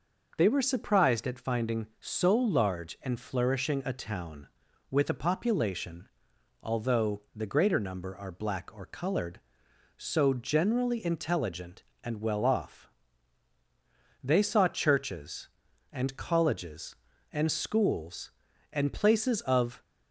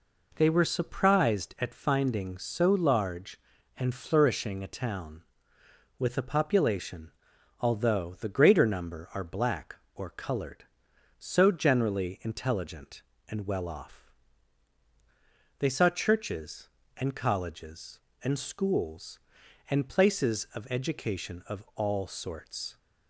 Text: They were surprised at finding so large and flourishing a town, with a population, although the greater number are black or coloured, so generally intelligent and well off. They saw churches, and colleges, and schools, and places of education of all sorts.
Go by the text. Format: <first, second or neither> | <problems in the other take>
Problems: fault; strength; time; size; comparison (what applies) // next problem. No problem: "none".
second | stops before "education of all sorts"; at 19.8 s